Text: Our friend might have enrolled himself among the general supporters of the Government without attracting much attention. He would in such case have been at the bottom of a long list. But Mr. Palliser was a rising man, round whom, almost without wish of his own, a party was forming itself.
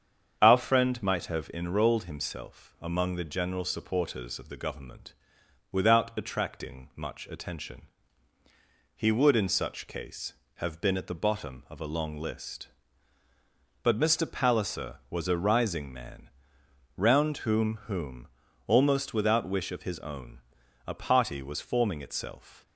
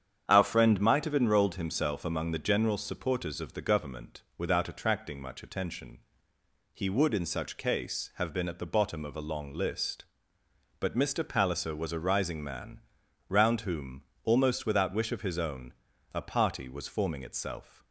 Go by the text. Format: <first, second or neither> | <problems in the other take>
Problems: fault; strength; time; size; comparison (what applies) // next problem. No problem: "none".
second | starts louder than the rest; strong; until 1.4 s; 7.5 dB; strong in the second // pauses between "Government" and "without"; noticeable; at 5.1 s; 0.58 s long; slight in the second // says "whom" twice; at 17.8 s